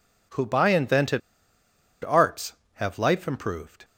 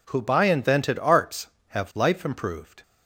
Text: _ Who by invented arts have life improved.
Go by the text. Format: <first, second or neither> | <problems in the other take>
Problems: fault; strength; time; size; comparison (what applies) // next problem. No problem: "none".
second | pauses between "invented" and "arts"; noticeable; at 1.2 s; 0.84 s long